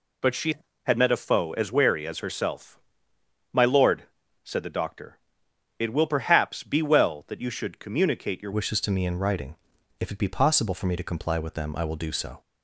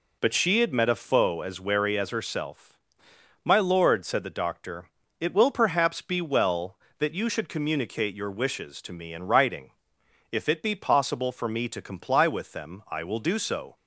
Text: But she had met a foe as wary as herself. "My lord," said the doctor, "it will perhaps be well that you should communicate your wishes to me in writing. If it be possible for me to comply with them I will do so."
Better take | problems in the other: second | changes voice at "wishes"; from 8.5 s on; 3.9 s long

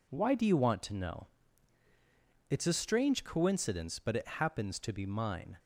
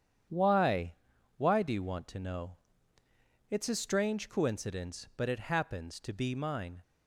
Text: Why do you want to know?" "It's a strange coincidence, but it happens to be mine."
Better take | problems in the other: first | starts louder than the rest; strong; until 1.7 s; 8.5 dB // says "Why" twice; at 1.3 s

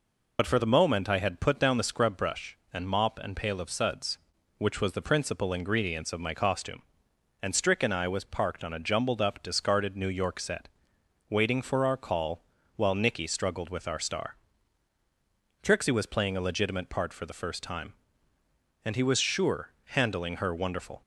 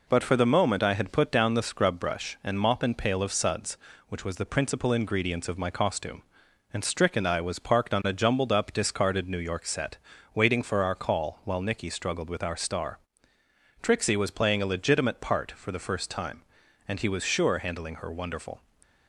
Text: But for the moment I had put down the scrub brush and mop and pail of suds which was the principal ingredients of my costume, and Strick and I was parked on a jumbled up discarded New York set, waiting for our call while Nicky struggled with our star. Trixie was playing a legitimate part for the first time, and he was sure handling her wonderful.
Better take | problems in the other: second | loses the start of "But"; at 0.3 s; 50 ms // pauses between "call" and "while"; slight; at 12.4 s; 0.32 s long // pauses between "sure" and "handling"; slight; at 19.6 s; 0.16 s long

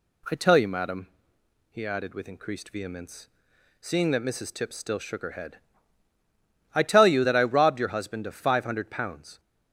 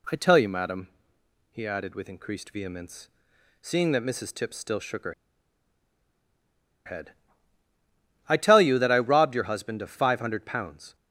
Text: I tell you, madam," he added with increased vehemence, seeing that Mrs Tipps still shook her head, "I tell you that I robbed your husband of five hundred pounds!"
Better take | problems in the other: first | pauses between "her" and "head"; strong; at 5.1 s; 1.7 s long

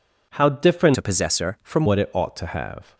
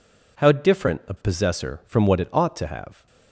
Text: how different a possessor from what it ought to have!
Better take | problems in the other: second | changes voice from "a" to "from"; from 0.9 to 1.8 s; 0.9 s long

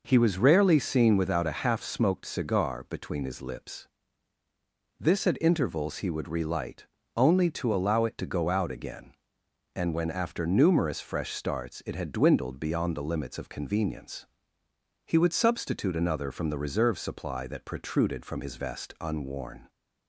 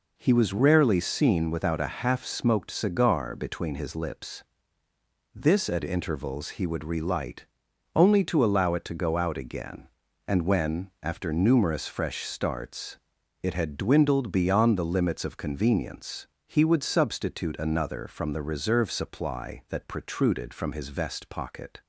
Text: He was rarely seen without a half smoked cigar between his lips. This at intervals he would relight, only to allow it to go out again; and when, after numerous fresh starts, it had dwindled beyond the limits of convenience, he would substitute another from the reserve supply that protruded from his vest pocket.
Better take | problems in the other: second | says "unworn" for "pocket"; at 19.0 s

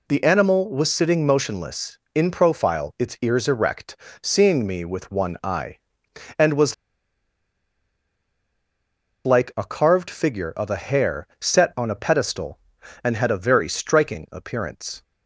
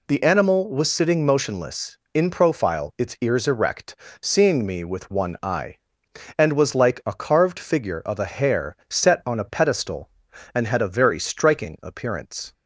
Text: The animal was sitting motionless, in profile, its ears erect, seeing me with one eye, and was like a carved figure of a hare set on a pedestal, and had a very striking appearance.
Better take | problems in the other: second | pauses between "was" and "like"; strong; at 6.7 s; 2.5 s long

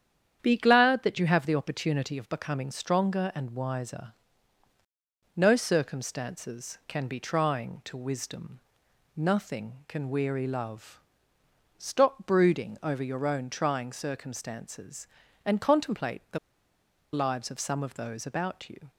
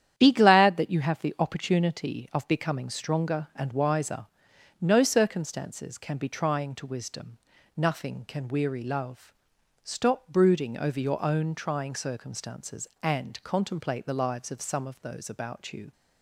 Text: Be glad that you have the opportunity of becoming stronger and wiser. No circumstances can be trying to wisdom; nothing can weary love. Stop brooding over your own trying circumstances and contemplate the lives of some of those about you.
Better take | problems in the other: second | starts louder than the rest; strong; until 1.4 s; 9 dB; strong in the second // pauses between "the" and "lives"; noticeable; at 16.3 s; 0.75 s long

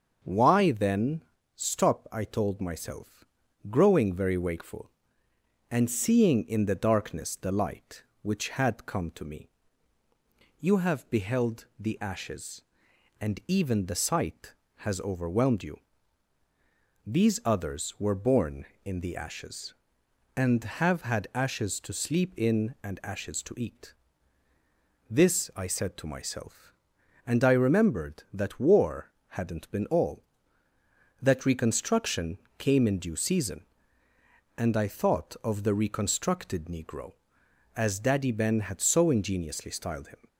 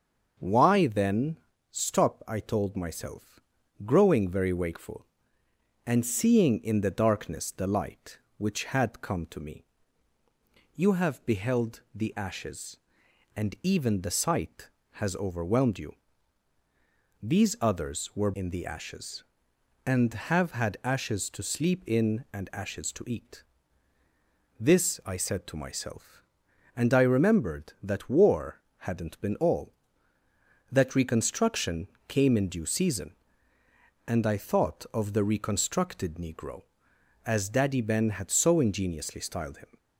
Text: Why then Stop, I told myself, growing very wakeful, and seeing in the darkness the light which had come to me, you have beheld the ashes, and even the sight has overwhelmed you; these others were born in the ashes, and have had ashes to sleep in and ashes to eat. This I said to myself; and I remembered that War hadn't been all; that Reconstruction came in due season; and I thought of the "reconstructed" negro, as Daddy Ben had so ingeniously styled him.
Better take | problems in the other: first | starts louder than the rest; until 1.7 s; 6.5 dB; also in the first // pauses between "then" and "Stop"; slight; at 1.3 s; 0.34 s long; slight in the first // skips "born"; at 18.3 s // pauses between "War" and "hadn't"; slight; at 28.6 s; 0.18 s long; slight in the first // pauses between "Reconstruction" and "came"; slight; at 31.8 s; 0.22 s long; slight in the first

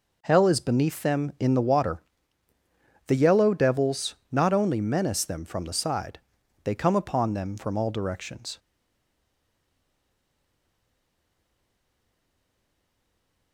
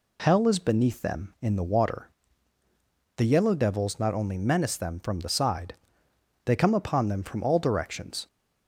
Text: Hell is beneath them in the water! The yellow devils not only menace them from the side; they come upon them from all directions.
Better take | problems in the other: second | pauses between "devils" and "not"; slight; at 4.1 s; 0.16 s long // stays silent after the last word; strong; from 8.5 s on; 5.0 s long

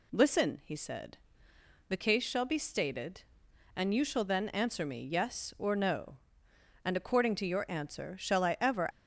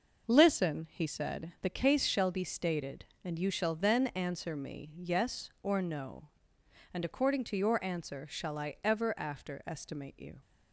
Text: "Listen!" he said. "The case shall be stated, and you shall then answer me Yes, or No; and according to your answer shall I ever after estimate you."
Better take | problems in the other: second | stops before "after estimate you"; at 8.9 s

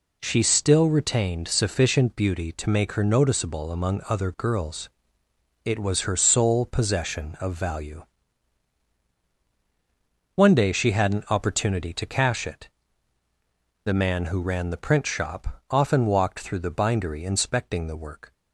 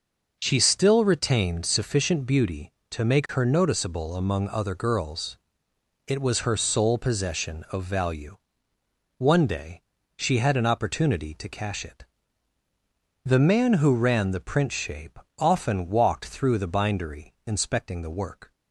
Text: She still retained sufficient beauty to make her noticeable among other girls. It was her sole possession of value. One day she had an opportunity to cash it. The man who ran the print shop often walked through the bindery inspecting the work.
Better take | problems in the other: first | pauses between "day" and "she"; slight; at 9.8 s; 0.36 s long // says "shape" for "shop"; at 14.7 s

